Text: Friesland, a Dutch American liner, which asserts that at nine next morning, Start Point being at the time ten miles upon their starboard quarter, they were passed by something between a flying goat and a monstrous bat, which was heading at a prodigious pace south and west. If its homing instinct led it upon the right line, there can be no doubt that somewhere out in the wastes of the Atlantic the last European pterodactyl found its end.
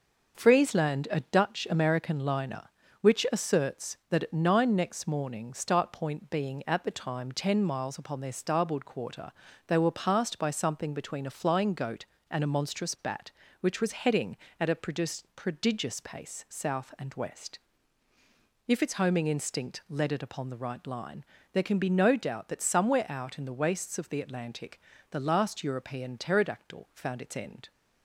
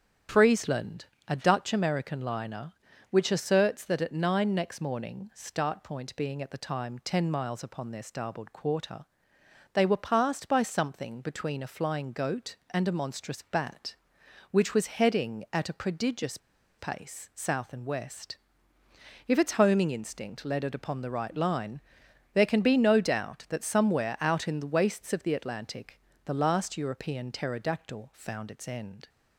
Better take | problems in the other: first | starts louder than the rest; strong; until 1.5 s; 8.5 dB // pauses between "prodigious" and "pace"; at 16.3 s; 0.40 s long // pauses between "Atlantic" and "the"; slight; at 25.9 s; 0.26 s long; slight in the first

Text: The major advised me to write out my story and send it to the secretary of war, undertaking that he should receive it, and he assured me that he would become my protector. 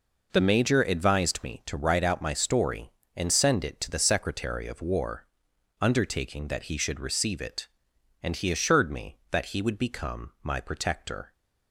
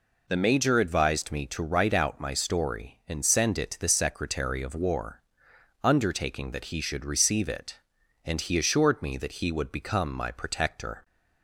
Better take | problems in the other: neither | none

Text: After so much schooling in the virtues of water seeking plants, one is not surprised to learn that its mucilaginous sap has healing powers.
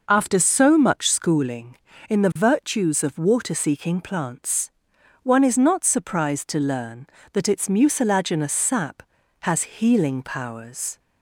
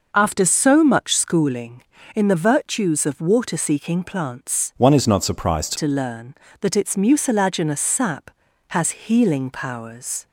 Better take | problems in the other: first | changes voice from "one" to "surprised"; from 4.7 to 5.7 s; 1.0 s long

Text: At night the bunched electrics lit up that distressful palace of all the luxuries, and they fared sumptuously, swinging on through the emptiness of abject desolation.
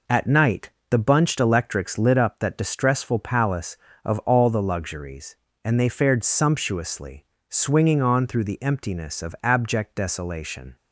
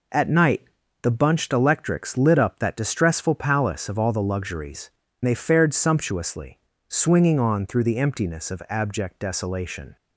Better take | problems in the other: first | pauses between "night" and "the"; at 0.6 s; 0.40 s long; slight in the first // skips "and"; at 5.0 s

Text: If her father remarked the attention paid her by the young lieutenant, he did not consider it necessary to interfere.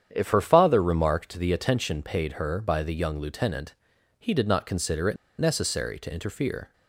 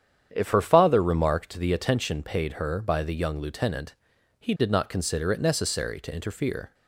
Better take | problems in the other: second | starts louder than the rest; strong; until 1.1 s; 9 dB; strong in the second // pauses between "it" and "necessary"; slight; at 5.1 s; 0.22 s long

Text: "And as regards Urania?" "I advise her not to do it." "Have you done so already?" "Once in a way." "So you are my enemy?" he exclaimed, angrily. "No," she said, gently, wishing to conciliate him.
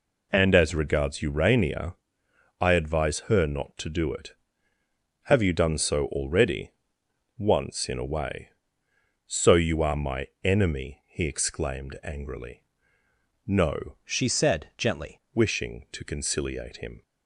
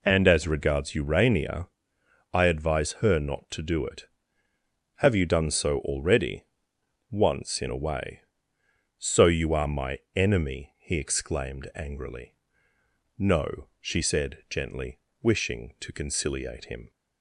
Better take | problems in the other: second | pauses between "my" and "enemy"; slight; at 10.2 s; 0.16 s long; slight in the second // changes voice from "she" to "gently"; from 14.0 to 15.1 s; 1.1 s long

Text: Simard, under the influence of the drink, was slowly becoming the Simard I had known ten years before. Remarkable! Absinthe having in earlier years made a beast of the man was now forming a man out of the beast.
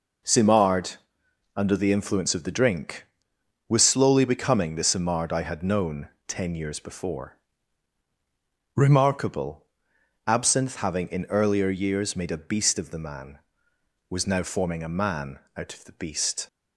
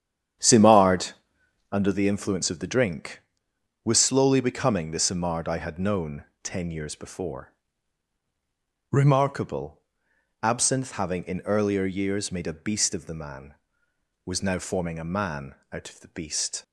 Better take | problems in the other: first | starts louder than the rest; strong; until 1.9 s; 9.5 dB // pauses between "known" and "ten"; slight; at 6.2 s; 0.22 s long; slight in the first // pauses between "man" and "out"; slight; at 15.5 s; 0.18 s long; slight in the first

